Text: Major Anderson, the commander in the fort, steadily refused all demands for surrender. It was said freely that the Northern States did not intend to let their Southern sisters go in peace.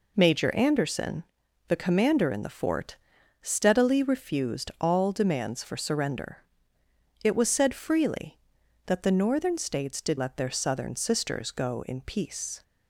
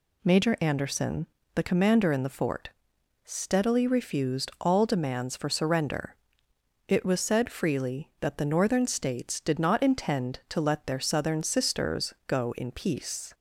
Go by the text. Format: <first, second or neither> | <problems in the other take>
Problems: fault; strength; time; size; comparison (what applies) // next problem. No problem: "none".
second | skips "not intend to"; at 10.1 s